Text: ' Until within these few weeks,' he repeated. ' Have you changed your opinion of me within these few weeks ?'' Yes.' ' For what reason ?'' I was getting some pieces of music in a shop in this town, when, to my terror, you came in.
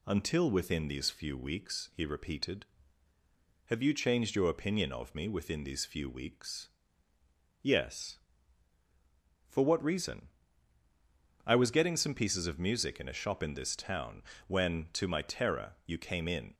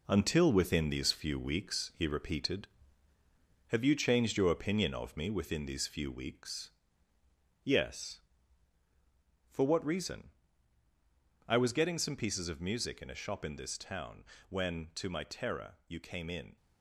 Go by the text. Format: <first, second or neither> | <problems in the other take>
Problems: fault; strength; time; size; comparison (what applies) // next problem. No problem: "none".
first | gets quieter; throughout; 6.5 dB